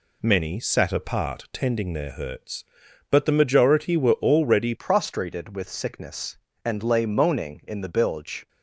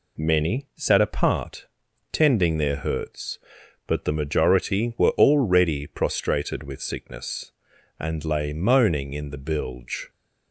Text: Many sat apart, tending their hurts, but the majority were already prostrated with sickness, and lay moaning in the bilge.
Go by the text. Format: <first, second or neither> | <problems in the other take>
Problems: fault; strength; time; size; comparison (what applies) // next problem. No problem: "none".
second | changes voice at "prostrated"; from 4.7 s on; 3.7 s long